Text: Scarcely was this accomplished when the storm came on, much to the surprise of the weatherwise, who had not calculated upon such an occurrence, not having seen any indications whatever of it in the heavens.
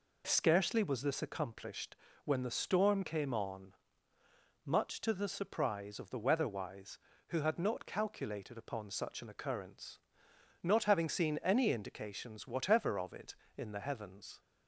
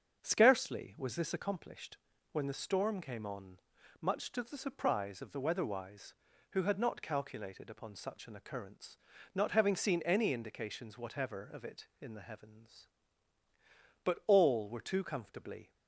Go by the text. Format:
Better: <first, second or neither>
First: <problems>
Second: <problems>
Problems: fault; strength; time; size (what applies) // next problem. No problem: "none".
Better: first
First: pauses between "accomplished" and "when"; slight; at 1.9 s; 0.30 s long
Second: starts louder than the rest; until 1.2 s; 7 dB // pauses between "accomplished" and "when"; slight; at 1.9 s; 0.34 s long // goes on to say "But all were too comfortably"; strong; from 14.0 s on; 1.6 s long